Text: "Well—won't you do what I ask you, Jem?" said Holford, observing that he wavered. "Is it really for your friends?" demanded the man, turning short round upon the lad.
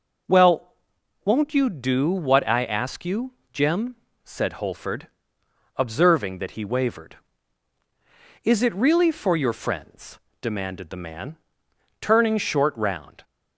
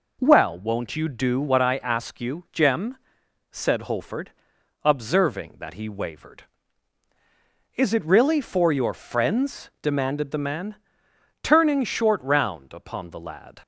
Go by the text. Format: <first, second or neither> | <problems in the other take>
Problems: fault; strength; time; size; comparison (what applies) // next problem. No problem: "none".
second | stops before "upon the lad"; at 13.2 s